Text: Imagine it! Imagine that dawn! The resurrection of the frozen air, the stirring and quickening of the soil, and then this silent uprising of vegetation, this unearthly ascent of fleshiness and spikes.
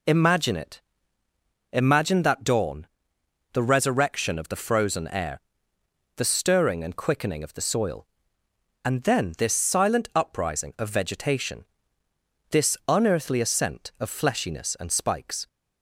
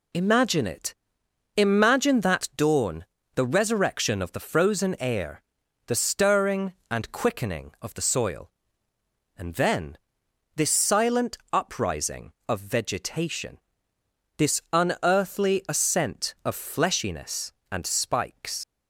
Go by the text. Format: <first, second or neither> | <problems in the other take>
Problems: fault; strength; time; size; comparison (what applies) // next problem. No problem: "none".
first | pauses between "then" and "this"; noticeable; at 9.9 s; 0.58 s long // leaves "spikes" unfinished; at 18.6 s; 80 ms